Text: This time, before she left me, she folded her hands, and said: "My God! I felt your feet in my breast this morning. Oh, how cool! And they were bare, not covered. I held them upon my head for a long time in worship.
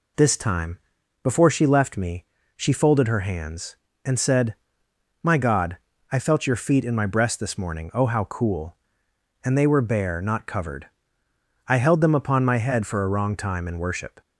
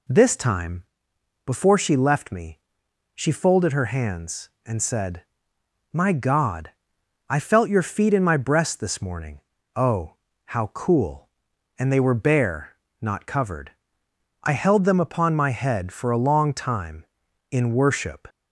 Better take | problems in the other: second | says "wrong" for "long"; at 13.0 s

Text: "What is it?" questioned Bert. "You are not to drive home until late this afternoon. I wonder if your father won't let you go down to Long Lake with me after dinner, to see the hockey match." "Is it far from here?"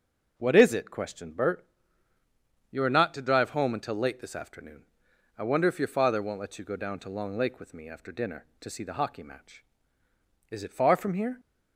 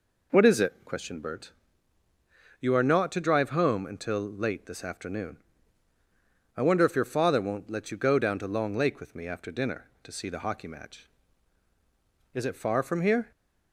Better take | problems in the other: neither | none

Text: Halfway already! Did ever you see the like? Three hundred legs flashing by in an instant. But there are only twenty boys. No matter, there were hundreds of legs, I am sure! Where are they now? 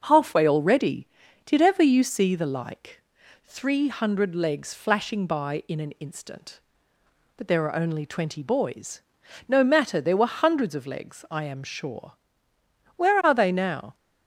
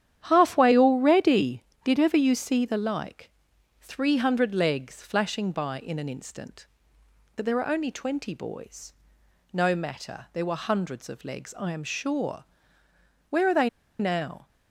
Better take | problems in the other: first | starts louder than the rest; strong; until 1.2 s; 10 dB; also in the first // pauses between "they" and "now"; slight; at 13.6 s; 0.31 s long

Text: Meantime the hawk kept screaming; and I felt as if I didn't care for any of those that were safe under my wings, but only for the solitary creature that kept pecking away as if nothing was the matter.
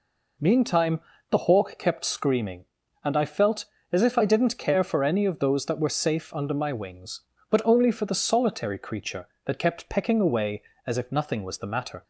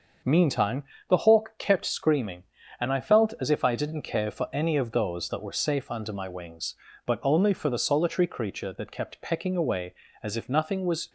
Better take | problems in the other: first | starts louder than the rest; until 1.5 s; 6.5 dB // pauses between "Meantime" and "the"; slight; at 0.8 s; 0.26 s long; slight in the first // stops before "the matter"; at 11.0 s

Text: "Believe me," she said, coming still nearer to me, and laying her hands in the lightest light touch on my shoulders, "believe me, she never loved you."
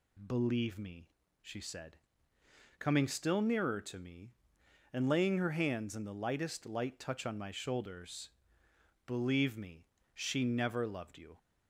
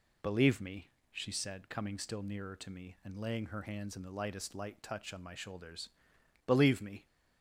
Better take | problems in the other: first | stops before "she never loved you"; at 7.0 s

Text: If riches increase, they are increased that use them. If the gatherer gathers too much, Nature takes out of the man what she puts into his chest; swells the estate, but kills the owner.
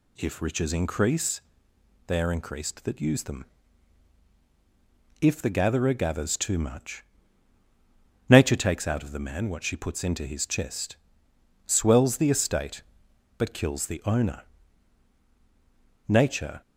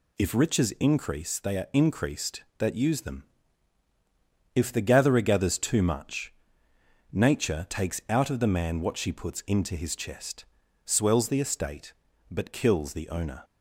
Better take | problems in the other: second | goes on to say "Nature"; from 16.0 s on; 0.54 s long

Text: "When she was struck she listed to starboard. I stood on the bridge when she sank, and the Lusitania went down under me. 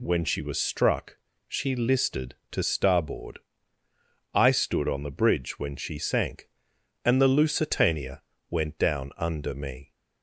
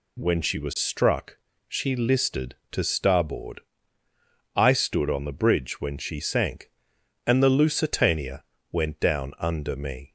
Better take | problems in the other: neither | pauses between "struck" and "she"; slight; the same in both // pauses between "Lusitania" and "went"; slight; the same in both

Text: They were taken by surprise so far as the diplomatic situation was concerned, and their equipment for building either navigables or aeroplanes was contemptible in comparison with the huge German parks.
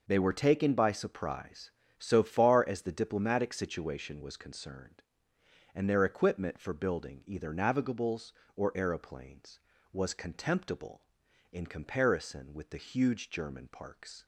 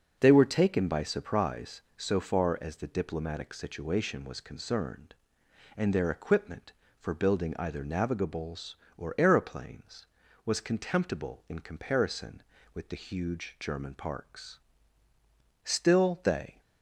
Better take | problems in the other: first | goes on to say "Still they"; noticeable; from 15.6 s on; 0.96 s long

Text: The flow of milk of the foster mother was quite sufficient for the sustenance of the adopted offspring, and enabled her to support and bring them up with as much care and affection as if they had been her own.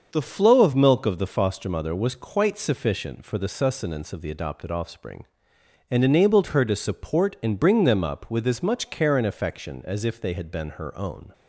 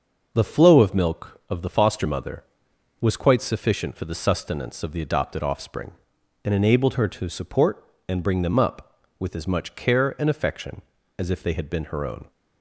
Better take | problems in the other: neither | starts louder than the rest; the same in both

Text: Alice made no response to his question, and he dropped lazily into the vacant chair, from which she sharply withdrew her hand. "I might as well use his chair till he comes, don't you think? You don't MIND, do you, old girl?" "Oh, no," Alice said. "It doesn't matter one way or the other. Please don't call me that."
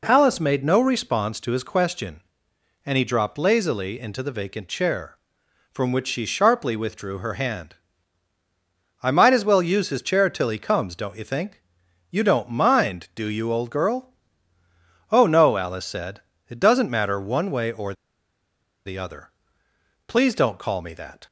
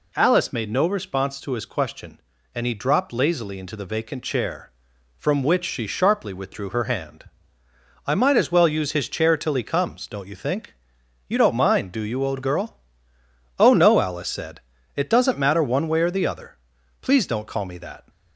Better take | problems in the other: second | pauses between "or" and "the"; noticeable; at 17.9 s; 0.91 s long

